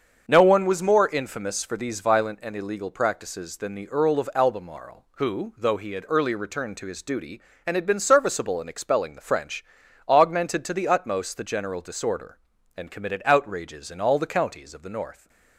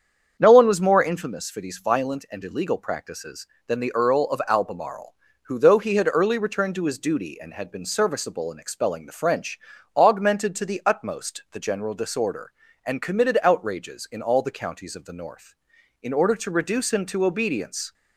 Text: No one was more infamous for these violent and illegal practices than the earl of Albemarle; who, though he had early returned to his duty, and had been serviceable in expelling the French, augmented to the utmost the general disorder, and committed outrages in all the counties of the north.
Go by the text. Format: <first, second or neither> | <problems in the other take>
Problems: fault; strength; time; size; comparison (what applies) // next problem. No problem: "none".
first | starts louder than the rest; strong; until 1.4 s; 7.5 dB; also in the first // goes on to say "In order to reduce him to obedience"; strong; from 16.0 s on; 1.9 s long